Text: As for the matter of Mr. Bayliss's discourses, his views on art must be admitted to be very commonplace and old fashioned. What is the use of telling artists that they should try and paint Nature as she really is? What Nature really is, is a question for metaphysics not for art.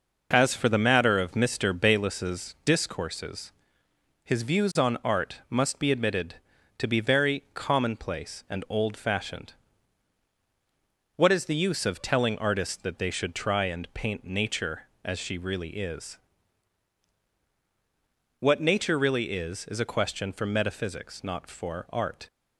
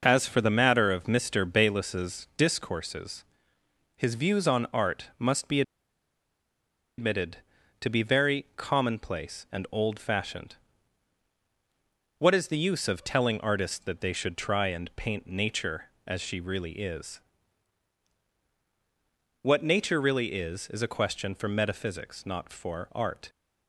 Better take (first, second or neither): first